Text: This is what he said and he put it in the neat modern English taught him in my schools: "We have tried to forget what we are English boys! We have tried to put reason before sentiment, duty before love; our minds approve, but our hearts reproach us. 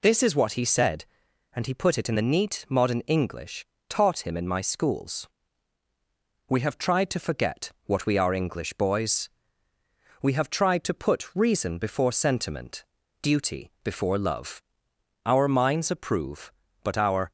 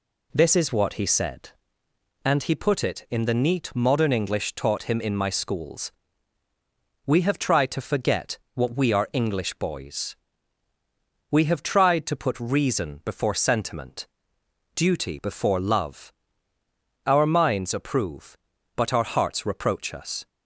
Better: second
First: pauses between "English" and "taught"; slight; at 3.6 s; 0.24 s long // pauses between "forget" and "what"; slight; at 7.7 s; 0.16 s long // stops before "hearts reproach us"; at 17.2 s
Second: pauses between "forget" and "what"; slight; at 8.3 s; 0.16 s long

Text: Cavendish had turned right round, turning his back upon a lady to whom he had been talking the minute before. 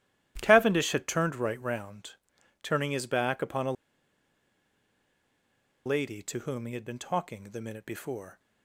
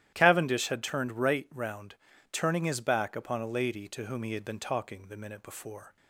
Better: second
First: starts louder than the rest; strong; until 1.4 s; 14 dB // pauses between "a" and "lady"; strong; at 3.7 s; 2.1 s long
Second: starts louder than the rest; strong; until 1.1 s; 12.5 dB

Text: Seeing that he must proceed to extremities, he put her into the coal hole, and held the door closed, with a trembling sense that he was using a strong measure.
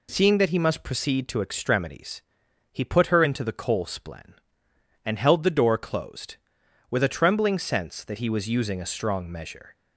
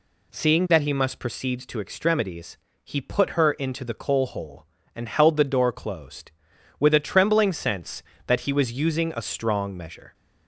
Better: second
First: says "splen" for "hole"; at 3.8 s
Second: none

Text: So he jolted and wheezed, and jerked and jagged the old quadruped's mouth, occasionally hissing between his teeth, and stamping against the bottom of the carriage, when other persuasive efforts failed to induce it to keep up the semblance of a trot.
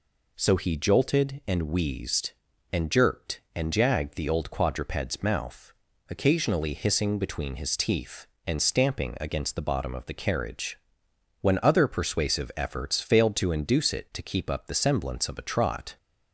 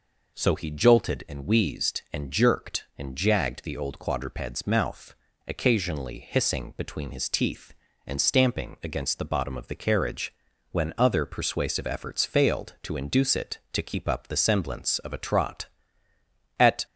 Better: first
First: none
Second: goes on to say "At"; slight; from 16.5 s on; 0.26 s long

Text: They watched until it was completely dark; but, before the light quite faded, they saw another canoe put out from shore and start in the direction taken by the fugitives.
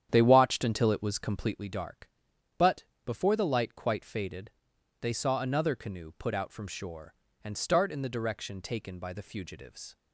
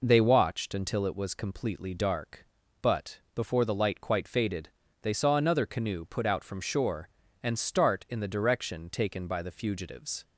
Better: second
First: starts louder than the rest; strong; until 1.6 s; 9.5 dB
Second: none

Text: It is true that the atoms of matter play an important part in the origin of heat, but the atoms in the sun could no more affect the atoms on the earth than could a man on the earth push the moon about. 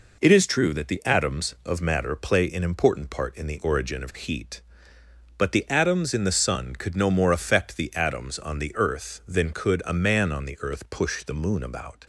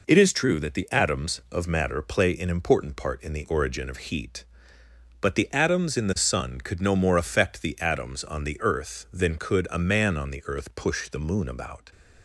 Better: neither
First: none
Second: none

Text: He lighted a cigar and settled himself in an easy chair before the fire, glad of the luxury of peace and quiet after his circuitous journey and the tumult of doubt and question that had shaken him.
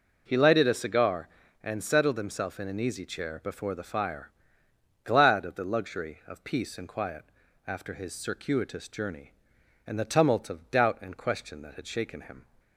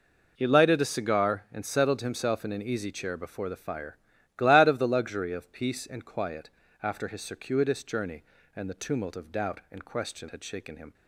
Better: first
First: pauses between "quiet" and "after"; at 7.2 s; 0.42 s long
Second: pauses between "quiet" and "after"; slight; at 6.4 s; 0.34 s long // skips "that"; at 10.2 s

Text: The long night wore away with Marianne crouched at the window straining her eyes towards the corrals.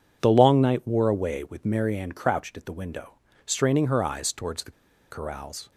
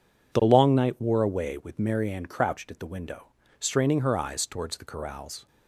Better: second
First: pauses between "window" and "straining"; slight; at 3.1 s; 0.32 s long // pauses between "the" and "corrals"; at 4.7 s; 0.39 s long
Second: pauses between "window" and "straining"; slight; at 3.2 s; 0.32 s long

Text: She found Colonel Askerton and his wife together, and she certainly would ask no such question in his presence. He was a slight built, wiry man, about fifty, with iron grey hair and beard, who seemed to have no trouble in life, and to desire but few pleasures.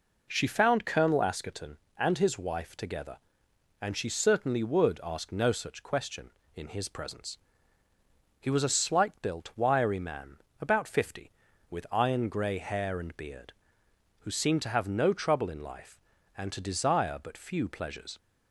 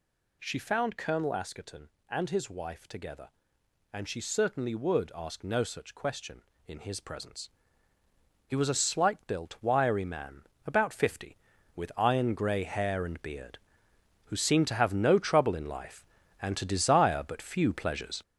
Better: first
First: none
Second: gets louder; throughout; 6.5 dB

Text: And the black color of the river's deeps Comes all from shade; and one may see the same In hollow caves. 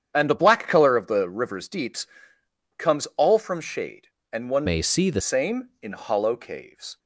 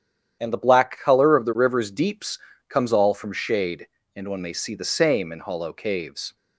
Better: second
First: starts louder than the rest; strong; until 1.1 s; 9 dB // pauses between "deeps" and "Comes"; noticeable; at 2.0 s; 0.70 s long // changes voice from "may" to "the"; from 4.6 to 5.2 s; 0.6 s long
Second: starts louder than the rest; strong; until 1.4 s; 9.5 dB // pauses between "deeps" and "Comes"; slight; at 2.3 s; 0.30 s long

